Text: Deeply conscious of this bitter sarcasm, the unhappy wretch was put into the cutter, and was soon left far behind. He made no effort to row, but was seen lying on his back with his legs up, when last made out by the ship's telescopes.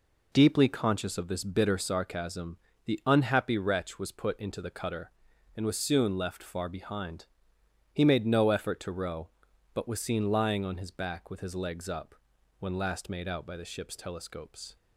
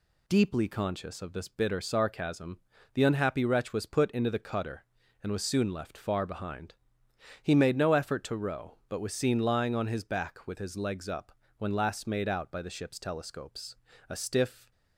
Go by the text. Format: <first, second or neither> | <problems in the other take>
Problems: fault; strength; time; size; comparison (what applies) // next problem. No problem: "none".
first | goes on to say "A stiff"; noticeable; from 14.0 s on; 0.62 s long